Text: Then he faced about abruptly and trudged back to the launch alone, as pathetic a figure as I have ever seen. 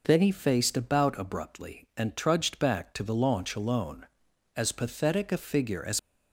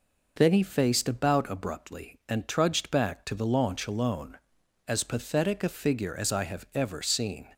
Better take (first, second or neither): second